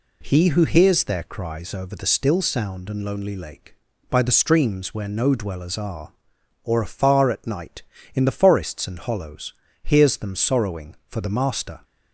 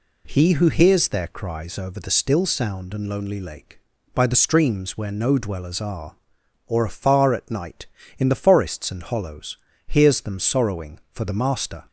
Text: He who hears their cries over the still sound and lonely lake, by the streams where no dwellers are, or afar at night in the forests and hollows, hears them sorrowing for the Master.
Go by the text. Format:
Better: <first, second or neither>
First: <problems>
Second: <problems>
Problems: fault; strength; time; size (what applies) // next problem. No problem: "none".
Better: neither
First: none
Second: none